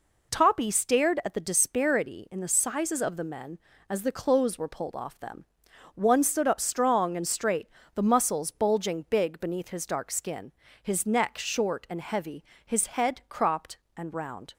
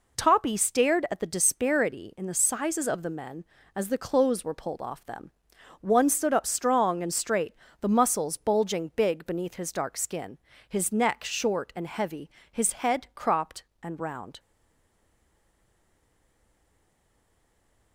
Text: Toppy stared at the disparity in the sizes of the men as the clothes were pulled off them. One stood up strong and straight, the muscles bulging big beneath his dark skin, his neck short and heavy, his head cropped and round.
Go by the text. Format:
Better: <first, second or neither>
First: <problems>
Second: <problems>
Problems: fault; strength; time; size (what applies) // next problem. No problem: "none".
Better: first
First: none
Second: stays silent after the last word; strong; from 14.3 s on; 3.6 s long